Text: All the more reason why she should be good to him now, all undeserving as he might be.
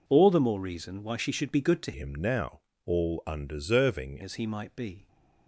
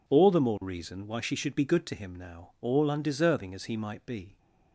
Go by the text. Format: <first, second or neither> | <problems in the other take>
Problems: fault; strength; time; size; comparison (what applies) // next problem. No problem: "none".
second | changes voice from "him" to "undeserving"; from 1.9 to 4.2 s; 2.3 s long